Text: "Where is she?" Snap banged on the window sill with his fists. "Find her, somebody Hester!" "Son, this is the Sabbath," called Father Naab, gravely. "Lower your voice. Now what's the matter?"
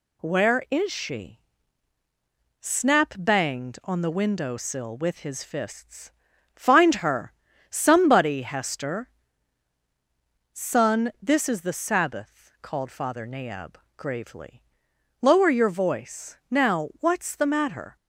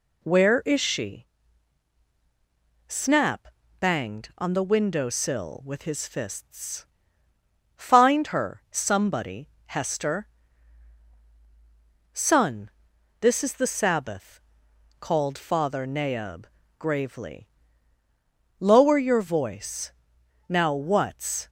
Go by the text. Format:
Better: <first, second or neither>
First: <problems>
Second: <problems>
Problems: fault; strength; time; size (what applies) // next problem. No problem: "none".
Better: first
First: none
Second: pauses between "Snap" and "banged"; slight; at 3.4 s; 0.32 s long // pauses between "somebody" and "Hester"; slight; at 9.4 s; 0.18 s long // stops before "the matter"; at 21.4 s